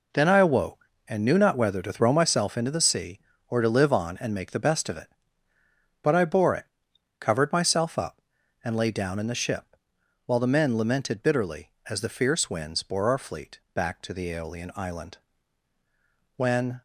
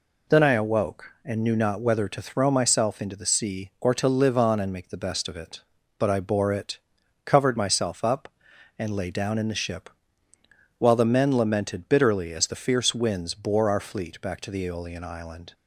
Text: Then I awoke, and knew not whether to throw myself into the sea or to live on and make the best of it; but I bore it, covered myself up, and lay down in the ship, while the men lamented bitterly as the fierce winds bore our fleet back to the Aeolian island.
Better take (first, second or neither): second